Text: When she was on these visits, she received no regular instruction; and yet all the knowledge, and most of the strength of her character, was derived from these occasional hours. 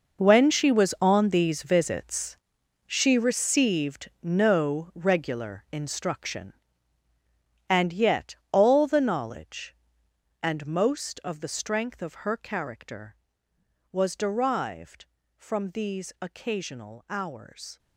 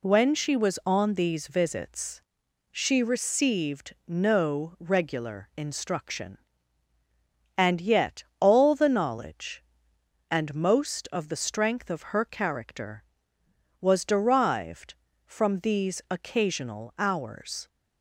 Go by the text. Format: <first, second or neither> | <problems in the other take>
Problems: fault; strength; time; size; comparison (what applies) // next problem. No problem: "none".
second | gets quieter; strong; throughout; 14.5 dB // pauses between "yet" and "all"; slight; at 8.3 s; 0.16 s long; slight in the second